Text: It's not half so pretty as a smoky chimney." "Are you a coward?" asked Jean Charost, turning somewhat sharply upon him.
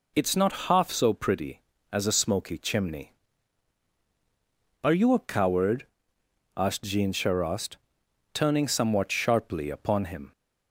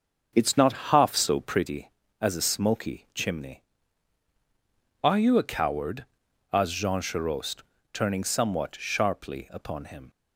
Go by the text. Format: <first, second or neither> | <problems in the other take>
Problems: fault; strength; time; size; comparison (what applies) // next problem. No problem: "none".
first | starts louder than the rest; until 1.7 s; 7 dB